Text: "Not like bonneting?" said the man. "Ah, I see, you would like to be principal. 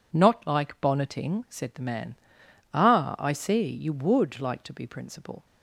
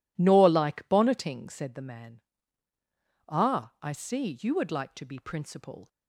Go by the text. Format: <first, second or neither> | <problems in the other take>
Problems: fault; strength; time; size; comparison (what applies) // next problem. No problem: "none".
first | says "Nor" for "Not"; at 0.1 s